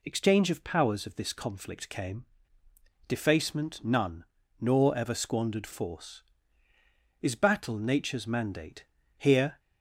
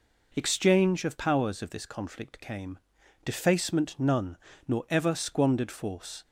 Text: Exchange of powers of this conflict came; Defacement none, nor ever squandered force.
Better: second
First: goes on to say "Is battle nature's mandate here"; strong; from 7.2 s on; 2.3 s long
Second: none

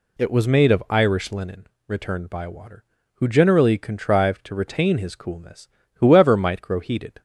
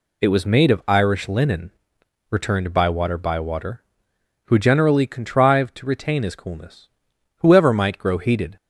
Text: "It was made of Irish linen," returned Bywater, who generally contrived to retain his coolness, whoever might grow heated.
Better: first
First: none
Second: says "Bywater" twice; at 3.1 s

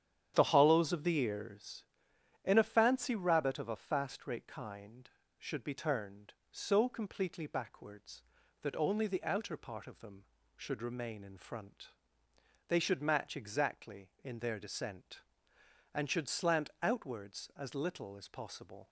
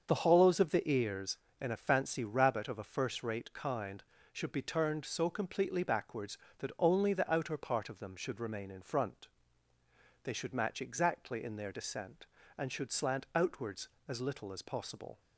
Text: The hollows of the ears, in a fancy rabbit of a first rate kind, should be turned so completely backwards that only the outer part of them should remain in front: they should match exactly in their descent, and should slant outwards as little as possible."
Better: second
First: starts louder than the rest; strong; until 1.3 s; 9.5 dB // says "fast" for "first"; at 3.7 s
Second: starts louder than the rest; until 1.1 s; 7 dB

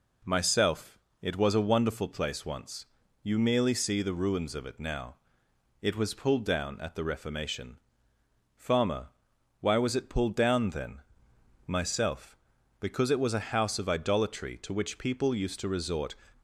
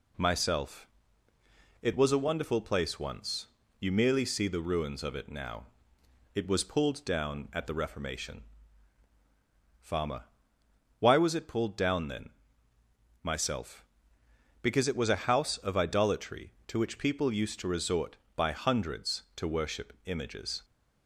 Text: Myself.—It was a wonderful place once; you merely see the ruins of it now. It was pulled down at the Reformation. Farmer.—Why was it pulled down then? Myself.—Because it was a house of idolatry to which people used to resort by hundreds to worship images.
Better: second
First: stops before "by hundreds to worship images"; at 16.3 s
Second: none

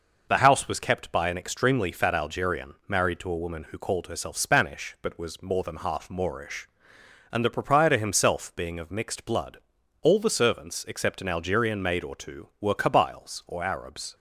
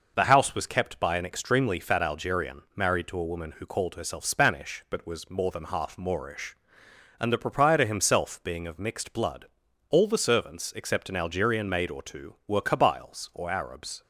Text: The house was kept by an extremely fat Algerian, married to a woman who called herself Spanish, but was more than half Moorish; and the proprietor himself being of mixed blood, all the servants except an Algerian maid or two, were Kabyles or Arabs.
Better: neither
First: none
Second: none

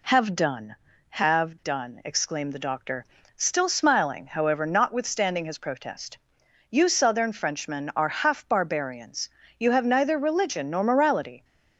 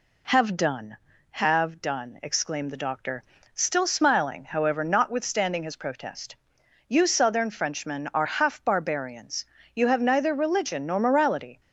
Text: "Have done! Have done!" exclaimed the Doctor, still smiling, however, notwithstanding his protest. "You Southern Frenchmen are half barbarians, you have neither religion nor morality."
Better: neither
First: none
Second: none

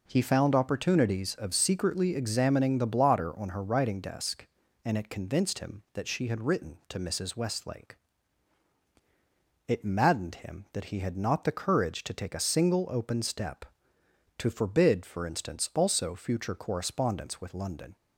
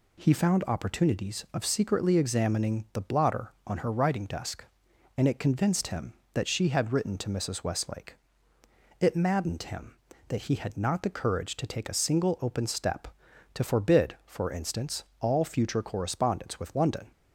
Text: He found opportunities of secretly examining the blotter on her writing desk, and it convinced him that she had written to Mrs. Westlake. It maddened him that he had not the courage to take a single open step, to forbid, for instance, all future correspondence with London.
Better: second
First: says "also" for "all"; at 15.7 s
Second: none

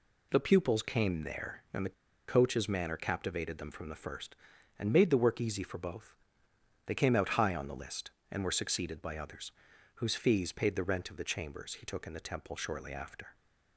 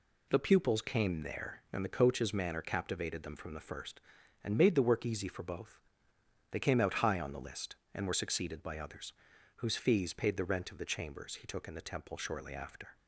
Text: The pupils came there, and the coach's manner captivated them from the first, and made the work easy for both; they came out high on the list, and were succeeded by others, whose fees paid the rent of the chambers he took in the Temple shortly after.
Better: second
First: pauses between "the" and "coach's"; at 1.9 s; 0.36 s long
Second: none

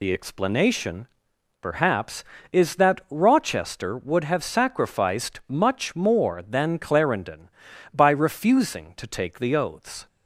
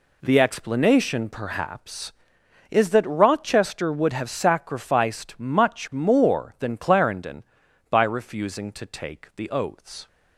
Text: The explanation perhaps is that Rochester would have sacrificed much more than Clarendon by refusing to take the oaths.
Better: second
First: loses the start of "The"; at 0.0 s; 60 ms // pauses between "explanation" and "perhaps"; noticeable; at 1.0 s; 0.54 s long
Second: none

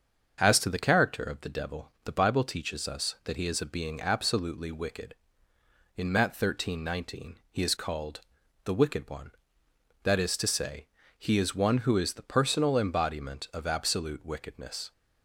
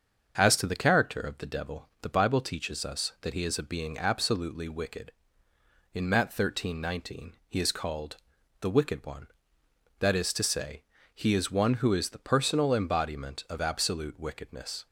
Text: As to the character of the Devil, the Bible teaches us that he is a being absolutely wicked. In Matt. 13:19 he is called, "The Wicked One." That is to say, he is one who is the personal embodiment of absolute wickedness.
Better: neither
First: starts louder than the rest; until 1.4 s; 6.5 dB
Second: starts louder than the rest; until 1.4 s; 6.5 dB

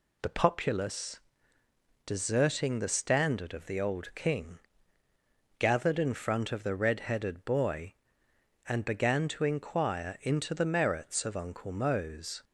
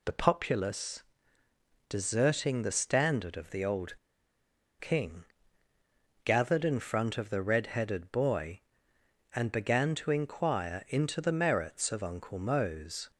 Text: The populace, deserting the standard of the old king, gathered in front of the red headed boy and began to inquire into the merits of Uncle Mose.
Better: first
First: none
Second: pauses between "old" and "king"; noticeable; at 3.9 s; 0.82 s long

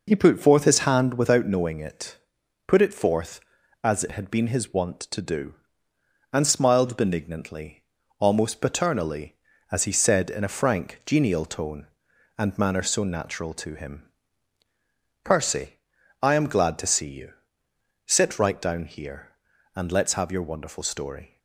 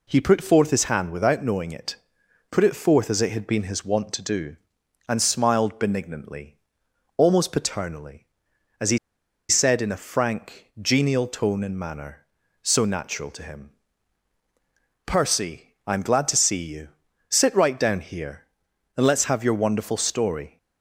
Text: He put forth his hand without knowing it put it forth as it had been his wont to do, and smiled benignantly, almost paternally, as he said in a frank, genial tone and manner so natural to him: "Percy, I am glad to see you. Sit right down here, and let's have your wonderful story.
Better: first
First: pauses between "it" and "put"; noticeable; at 2.1 s; 0.50 s long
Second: pauses between "it" and "put"; noticeable; at 1.9 s; 0.54 s long // pauses between "he" and "said"; noticeable; at 8.9 s; 0.52 s long

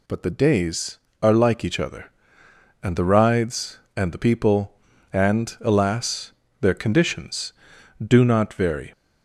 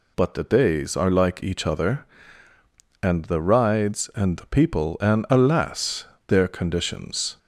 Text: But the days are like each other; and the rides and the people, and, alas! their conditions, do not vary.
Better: first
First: none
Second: stops before "do not vary"; at 7.3 s

